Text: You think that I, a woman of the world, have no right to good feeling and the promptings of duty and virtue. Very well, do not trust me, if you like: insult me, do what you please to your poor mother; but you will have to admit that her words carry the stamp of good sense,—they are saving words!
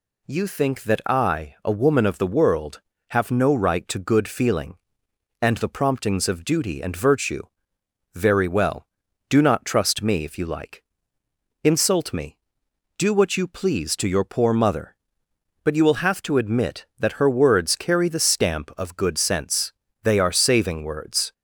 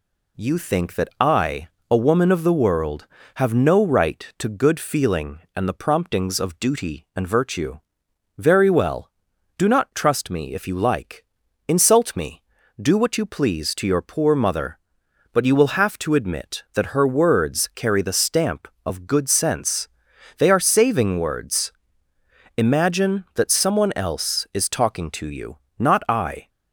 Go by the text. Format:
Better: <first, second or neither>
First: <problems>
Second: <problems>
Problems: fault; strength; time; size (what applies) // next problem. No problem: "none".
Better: first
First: none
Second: goes on to say "Imagine that someone else is talking to you not I"; strong; from 22.5 s on; 3.9 s long